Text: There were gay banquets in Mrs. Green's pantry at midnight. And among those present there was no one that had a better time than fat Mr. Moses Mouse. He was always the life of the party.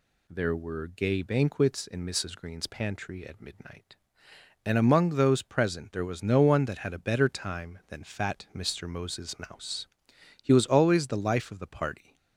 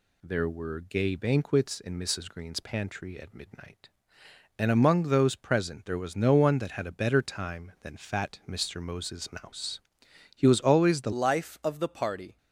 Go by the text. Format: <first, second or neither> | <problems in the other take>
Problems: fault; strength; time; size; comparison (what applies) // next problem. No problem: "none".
first | changes voice at "life"; from 11.1 s on; 1.2 s long